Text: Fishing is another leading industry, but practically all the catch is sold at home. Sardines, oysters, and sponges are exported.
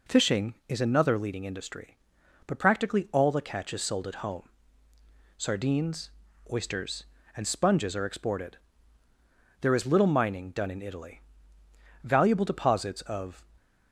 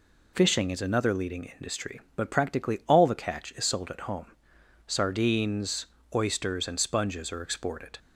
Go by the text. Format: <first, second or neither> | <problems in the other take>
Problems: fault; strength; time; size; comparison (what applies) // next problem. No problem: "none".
second | goes on to say "There is little mining done in Italy Valuable deposits of"; strong; from 9.5 s on; 3.8 s long